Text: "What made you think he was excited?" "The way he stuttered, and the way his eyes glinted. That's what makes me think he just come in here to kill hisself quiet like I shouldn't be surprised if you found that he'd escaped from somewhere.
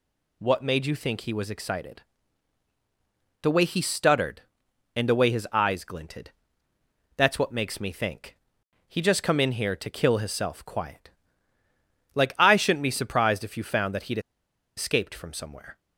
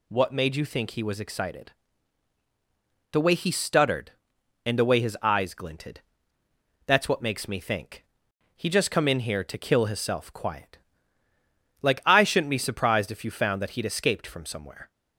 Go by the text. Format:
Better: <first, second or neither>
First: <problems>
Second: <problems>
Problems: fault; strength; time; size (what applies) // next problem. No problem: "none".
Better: second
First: pauses between "think" and "he"; noticeable; at 8.3 s; 0.50 s long // pauses between "quiet" and "like"; at 11.0 s; 1.0 s long // pauses between "he'd" and "escaped"; noticeable; at 14.1 s; 0.58 s long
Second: pauses between "think" and "he"; noticeable; at 8.0 s; 0.50 s long // pauses between "quiet" and "like"; at 10.7 s; 1.0 s long